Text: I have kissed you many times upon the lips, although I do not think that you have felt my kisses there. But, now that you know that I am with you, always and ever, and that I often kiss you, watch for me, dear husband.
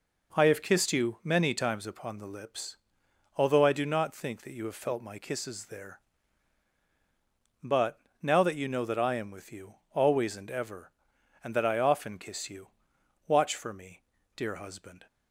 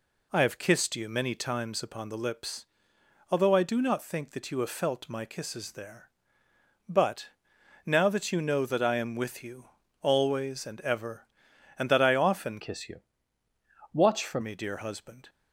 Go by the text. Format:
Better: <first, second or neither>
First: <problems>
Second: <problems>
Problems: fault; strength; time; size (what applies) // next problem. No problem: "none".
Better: first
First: none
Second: changes voice from "kiss" to "for"; from 12.6 to 14.4 s; 1.8 s long